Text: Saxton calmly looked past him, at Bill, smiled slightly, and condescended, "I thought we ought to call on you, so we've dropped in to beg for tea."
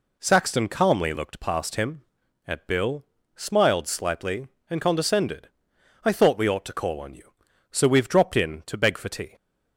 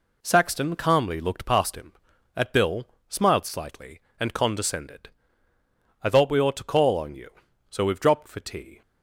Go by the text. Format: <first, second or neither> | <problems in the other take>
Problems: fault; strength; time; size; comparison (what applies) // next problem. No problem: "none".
first | skips "in to beg"; at 8.2 s